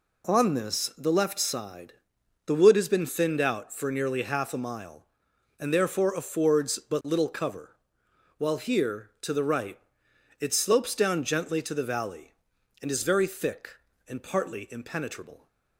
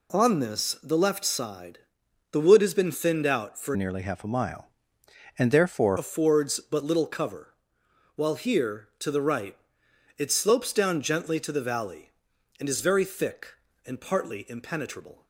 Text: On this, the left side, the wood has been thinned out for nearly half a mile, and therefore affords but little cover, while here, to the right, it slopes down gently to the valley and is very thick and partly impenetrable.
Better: first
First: none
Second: changes voice from "nearly" to "therefore"; from 3.7 to 5.9 s; 2.2 s long

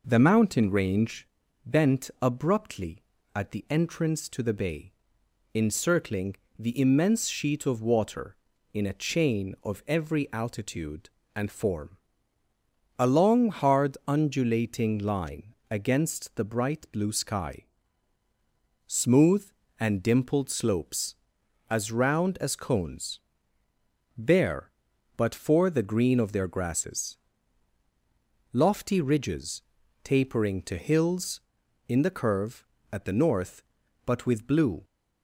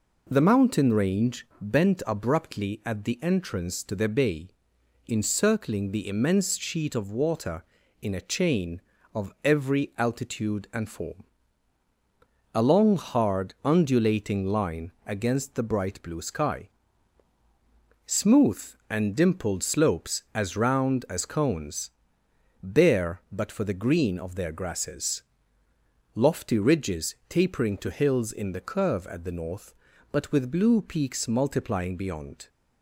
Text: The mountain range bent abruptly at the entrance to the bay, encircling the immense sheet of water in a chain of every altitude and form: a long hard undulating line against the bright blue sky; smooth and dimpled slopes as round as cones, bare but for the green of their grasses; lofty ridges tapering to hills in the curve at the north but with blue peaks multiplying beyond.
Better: second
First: pauses between "range" and "bent"; at 1.2 s; 0.38 s long // pauses between "encircling" and "the"; slight; at 6.3 s; 0.24 s long // pauses between "line" and "against"; slight; at 15.5 s; 0.16 s long // pauses between "ridges" and "tapering"; at 29.6 s; 0.40 s long // stops before "peaks multiplying beyond"; at 34.8 s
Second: none

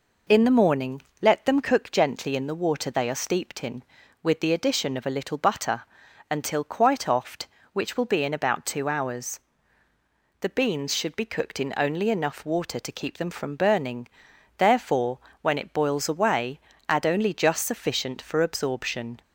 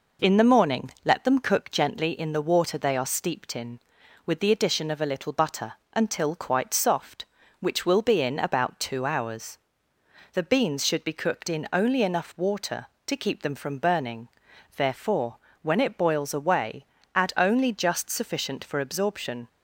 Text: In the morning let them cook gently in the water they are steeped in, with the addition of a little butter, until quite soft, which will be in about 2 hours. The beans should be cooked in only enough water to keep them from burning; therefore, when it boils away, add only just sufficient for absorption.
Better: second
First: pauses between "morning" and "let"; slight; at 0.9 s; 0.22 s long // says "oft" for "soft"; at 7.0 s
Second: none

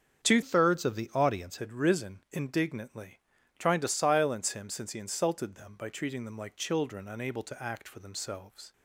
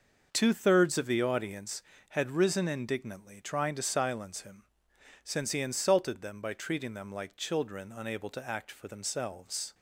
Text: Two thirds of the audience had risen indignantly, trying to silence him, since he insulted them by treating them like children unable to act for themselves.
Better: second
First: starts louder than the rest; strong; until 1.3 s; 7.5 dB // changes voice from "thirds" to "audience"; from 0.4 to 1.5 s; 1.1 s long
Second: none

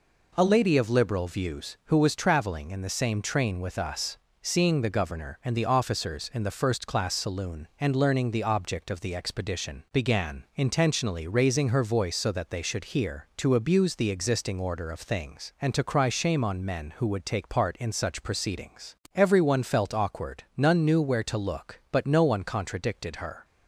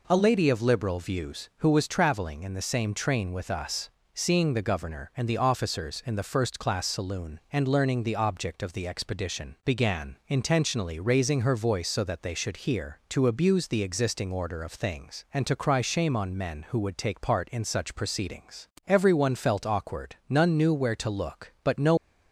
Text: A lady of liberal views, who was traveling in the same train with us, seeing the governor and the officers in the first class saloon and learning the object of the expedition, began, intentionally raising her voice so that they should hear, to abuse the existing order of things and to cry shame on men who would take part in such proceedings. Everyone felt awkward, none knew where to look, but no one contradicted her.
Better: first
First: none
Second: stops before "one contradicted her"; at 21.9 s

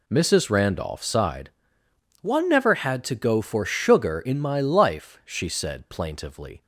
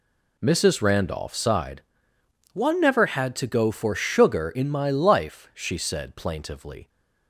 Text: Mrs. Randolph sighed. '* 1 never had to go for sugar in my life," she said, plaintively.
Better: neither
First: none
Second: none

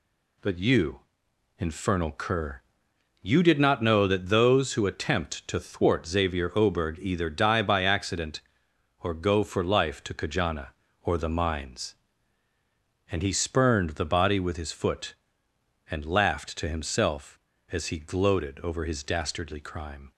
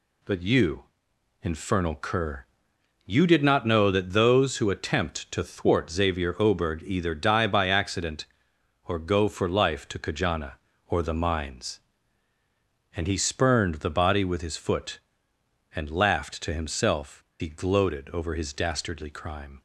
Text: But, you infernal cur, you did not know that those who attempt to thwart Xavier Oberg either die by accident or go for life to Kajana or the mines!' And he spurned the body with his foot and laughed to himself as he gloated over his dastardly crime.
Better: first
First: pauses between "you" and "infernal"; noticeable; at 0.9 s; 0.60 s long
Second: pauses between "you" and "infernal"; noticeable; at 0.8 s; 0.60 s long // skips "as"; at 17.3 s

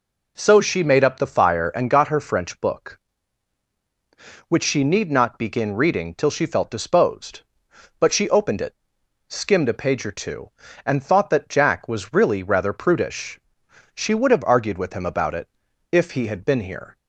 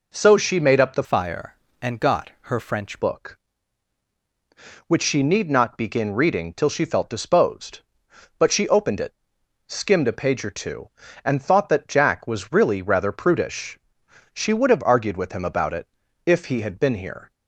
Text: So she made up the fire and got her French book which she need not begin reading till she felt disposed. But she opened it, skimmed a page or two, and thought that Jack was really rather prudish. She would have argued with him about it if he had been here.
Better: first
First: pauses between "it" and "if"; at 15.4 s; 0.42 s long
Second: changes voice from "fire" to "French"; from 1.0 to 3.0 s; 2.0 s long // pauses between "it" and "if"; at 15.8 s; 0.38 s long

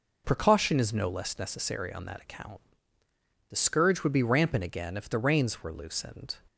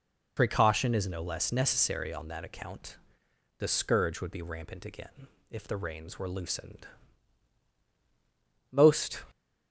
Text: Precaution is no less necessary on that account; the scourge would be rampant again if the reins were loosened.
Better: first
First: none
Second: pauses between "again" and "if"; slight; at 5.2 s; 0.24 s long // goes on to say "Most"; from 8.6 s on; 0.54 s long

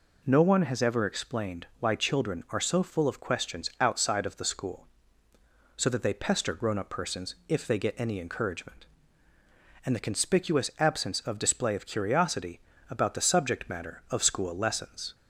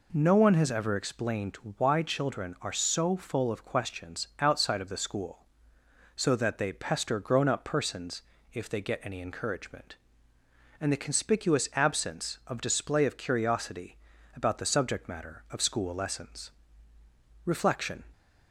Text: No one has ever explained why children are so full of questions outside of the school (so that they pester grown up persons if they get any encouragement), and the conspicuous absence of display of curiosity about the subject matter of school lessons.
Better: first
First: pauses between "curiosity" and "about"; slight; at 12.6 s; 0.28 s long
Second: pauses between "explained" and "why"; slight; at 1.5 s; 0.20 s long // pauses between "persons" and "if"; slight; at 8.2 s; 0.32 s long // pauses between "curiosity" and "about"; slight; at 13.9 s; 0.36 s long // goes on to say "Reflection"; from 17.4 s on; 0.58 s long

